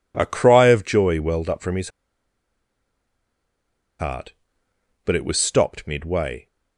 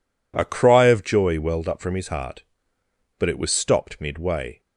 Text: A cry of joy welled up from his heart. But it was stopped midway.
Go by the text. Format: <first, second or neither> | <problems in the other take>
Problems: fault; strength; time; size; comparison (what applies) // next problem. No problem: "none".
second | pauses between "his" and "heart"; strong; at 1.8 s; 2.0 s long